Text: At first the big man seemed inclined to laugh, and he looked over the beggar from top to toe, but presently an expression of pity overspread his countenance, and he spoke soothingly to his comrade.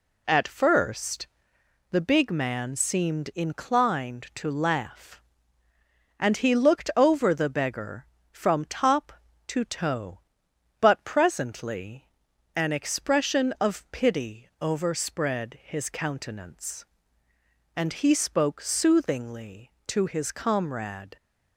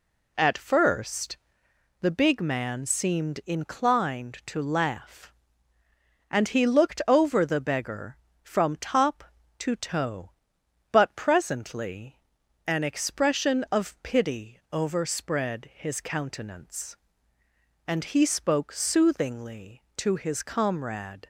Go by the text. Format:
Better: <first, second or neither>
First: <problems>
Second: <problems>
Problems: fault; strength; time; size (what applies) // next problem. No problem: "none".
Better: neither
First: pauses between "first" and "the"; noticeable; at 1.2 s; 0.64 s long // pauses between "presently" and "an"; noticeable; at 12.0 s; 0.48 s long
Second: pauses between "first" and "the"; noticeable; at 1.3 s; 0.64 s long // pauses between "presently" and "an"; noticeable; at 12.1 s; 0.48 s long